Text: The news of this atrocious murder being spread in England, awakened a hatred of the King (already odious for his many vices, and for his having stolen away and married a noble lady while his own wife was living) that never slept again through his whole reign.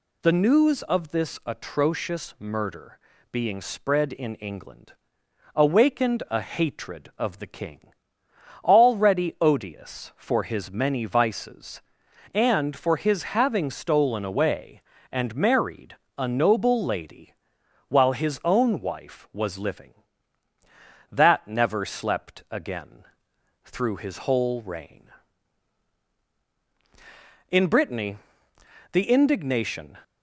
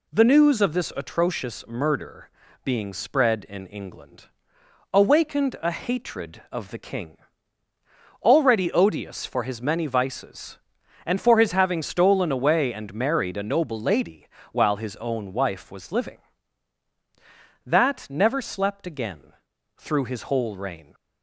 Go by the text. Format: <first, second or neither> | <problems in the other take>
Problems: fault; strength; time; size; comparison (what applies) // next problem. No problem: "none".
second | pauses between "murder" and "being"; slight; at 2.9 s; 0.32 s long; slight in the second // pauses between "married" and "a"; slight; at 15.9 s; 0.24 s long // pauses between "lady" and "while"; noticeable; at 17.3 s; 0.54 s long; slight in the second // pauses between "again" and "through"; noticeable; at 23.0 s; 0.60 s long; also in the second // goes on to say "In Brittany the indignation"; strong; from 27.4 s on; 2.4 s long